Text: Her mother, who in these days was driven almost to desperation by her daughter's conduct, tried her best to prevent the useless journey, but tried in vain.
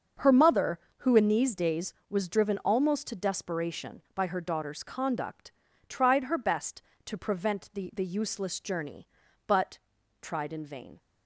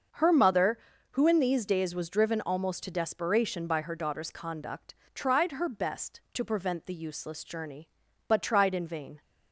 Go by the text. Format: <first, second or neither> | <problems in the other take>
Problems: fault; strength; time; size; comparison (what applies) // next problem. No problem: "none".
second | starts louder than the rest; until 1.3 s; 6.5 dB; also in the second // says "the" twice; at 7.9 s // pauses between "but" and "tried"; at 9.7 s; 0.42 s long